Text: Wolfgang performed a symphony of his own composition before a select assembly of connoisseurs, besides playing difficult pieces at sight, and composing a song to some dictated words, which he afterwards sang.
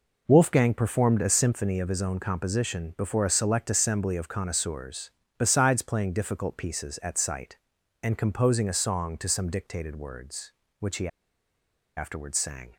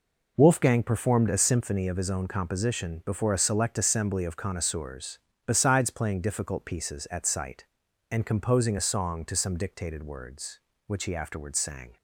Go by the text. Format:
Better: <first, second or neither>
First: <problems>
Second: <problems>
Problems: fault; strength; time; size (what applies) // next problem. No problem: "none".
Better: second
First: pauses between "he" and "afterwards"; noticeable; at 11.0 s; 0.89 s long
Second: none